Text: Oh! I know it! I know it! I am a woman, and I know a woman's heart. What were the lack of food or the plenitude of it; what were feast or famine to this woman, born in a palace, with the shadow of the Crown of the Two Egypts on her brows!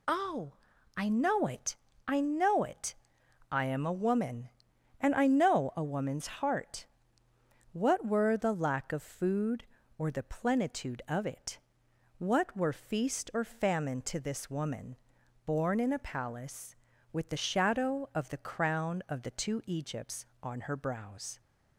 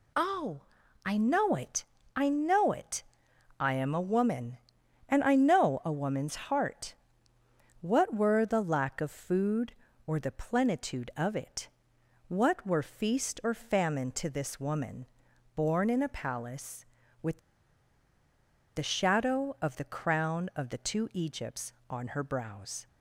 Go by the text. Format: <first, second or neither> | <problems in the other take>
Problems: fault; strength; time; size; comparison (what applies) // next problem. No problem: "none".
first | pauses between "with" and "the"; strong; at 17.3 s; 1.3 s long